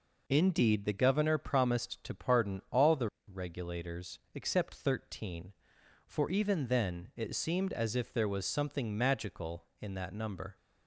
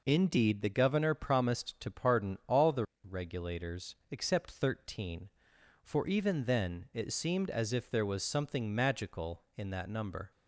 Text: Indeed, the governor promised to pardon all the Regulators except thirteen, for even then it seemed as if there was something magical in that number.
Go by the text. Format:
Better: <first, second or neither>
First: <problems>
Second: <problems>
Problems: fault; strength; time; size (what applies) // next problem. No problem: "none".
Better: neither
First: pauses between "the" and "Regulators"; slight; at 3.0 s; 0.24 s long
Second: pauses between "the" and "Regulators"; slight; at 2.8 s; 0.24 s long